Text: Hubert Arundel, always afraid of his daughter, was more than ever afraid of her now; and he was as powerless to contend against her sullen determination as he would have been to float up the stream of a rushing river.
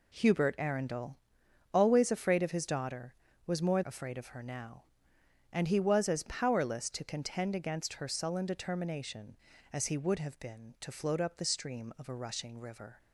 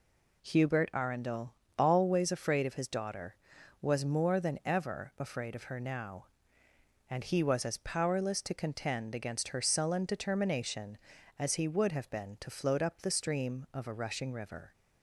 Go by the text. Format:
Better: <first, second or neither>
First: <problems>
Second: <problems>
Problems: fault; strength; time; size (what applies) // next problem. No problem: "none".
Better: second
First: skips "than ever"; at 3.8 s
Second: none